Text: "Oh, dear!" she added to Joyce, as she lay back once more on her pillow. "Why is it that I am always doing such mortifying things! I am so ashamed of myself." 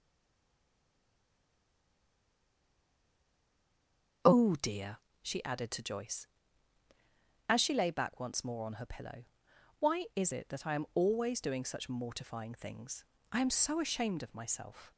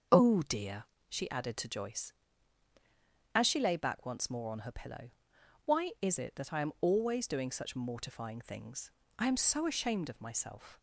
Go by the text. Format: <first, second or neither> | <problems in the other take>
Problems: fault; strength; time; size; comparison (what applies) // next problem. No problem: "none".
second | stays silent before the first word; strong; until 4.2 s; 4.2 s long // starts louder than the rest; until 5.4 s; 6.5 dB; also in the second